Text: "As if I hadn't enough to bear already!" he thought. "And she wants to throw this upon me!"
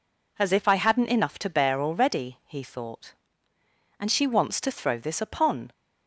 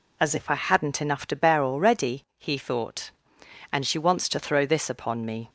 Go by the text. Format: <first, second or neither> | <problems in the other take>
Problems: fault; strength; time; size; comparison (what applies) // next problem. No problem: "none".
second | stops before "me"; at 5.7 s